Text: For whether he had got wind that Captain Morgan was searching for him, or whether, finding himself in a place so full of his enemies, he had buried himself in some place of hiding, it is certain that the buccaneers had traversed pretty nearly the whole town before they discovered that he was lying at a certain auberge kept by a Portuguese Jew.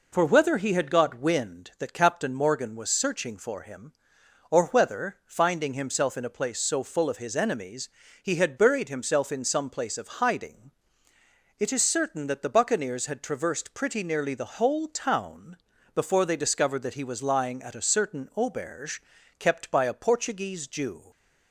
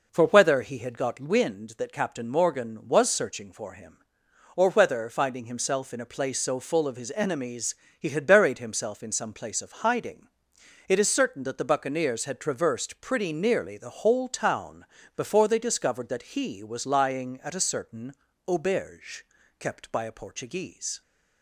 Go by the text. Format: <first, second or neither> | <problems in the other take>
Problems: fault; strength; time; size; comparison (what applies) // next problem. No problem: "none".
first | pauses between "town" and "before"; slight; at 14.8 s; 0.33 s long; also in the first // pauses between "certain" and "auberge"; slight; at 18.1 s; 0.34 s long // pauses between "auberge" and "kept"; slight; at 19.2 s; 0.34 s long; also in the first // stops before "Jew"; at 21.0 s